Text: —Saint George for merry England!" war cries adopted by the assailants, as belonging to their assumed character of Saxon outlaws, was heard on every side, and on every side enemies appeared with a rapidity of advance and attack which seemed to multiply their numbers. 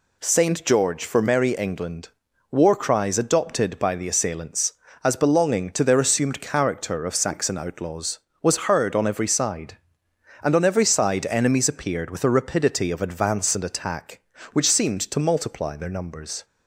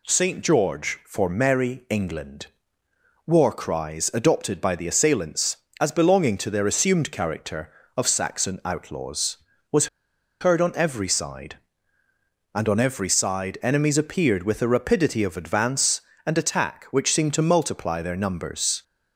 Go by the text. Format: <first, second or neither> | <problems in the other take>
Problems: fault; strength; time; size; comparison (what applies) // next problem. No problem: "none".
first | pauses between "was" and "heard"; noticeable; at 9.8 s; 0.53 s long